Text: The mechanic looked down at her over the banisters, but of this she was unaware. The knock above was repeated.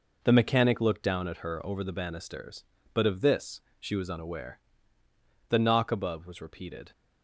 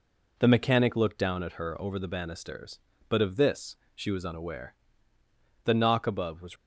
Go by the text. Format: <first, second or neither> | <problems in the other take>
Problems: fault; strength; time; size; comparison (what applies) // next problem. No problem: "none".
first | pauses between "this" and "she"; slight; at 3.7 s; 0.20 s long; slight in the first // stops before "repeated"; at 6.5 s